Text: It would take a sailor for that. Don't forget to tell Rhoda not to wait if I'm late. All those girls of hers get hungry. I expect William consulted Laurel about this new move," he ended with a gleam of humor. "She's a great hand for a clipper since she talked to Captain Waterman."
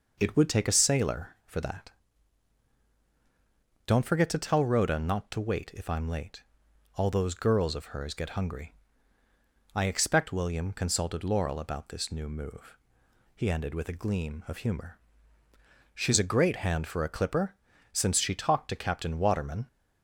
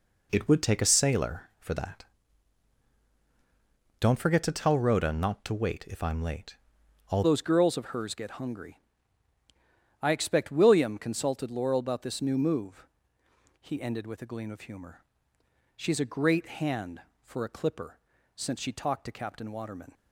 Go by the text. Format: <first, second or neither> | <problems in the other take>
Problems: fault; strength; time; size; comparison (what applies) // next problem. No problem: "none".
first | changes voice at "those"; from 7.2 s on; 12.7 s long // pauses between "clipper" and "since"; at 17.9 s; 0.38 s long; also in the first